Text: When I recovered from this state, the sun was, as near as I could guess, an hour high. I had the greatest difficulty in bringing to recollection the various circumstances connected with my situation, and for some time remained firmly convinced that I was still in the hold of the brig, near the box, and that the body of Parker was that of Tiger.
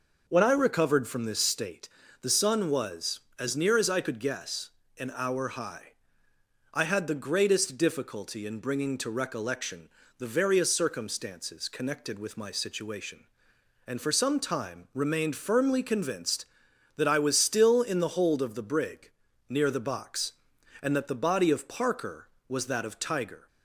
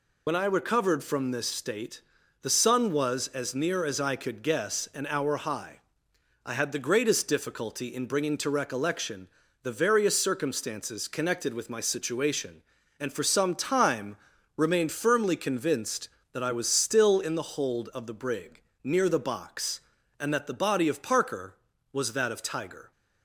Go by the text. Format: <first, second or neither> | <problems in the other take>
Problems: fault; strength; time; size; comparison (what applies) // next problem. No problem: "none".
first | loses the start of "When"; at 0.2 s; 60 ms // pauses between "recollection" and "the"; slight; at 9.2 s; 0.34 s long; slight in the first // pauses between "time" and "remained"; at 14.1 s; 0.40 s long